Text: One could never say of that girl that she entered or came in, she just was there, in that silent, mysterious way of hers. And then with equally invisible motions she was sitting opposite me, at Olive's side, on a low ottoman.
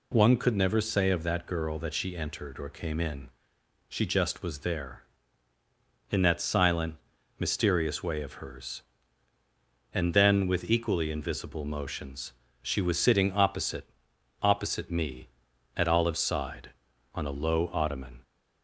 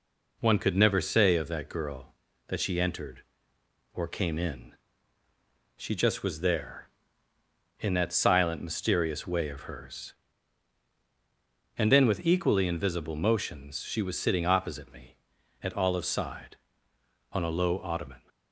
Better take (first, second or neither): second